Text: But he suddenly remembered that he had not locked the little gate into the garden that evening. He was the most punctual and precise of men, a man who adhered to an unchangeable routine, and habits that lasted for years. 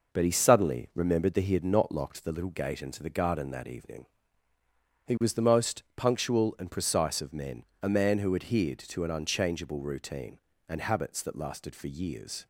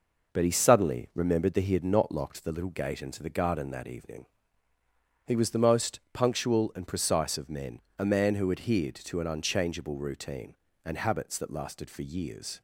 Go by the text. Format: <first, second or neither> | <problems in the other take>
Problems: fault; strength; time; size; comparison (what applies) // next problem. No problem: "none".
neither | none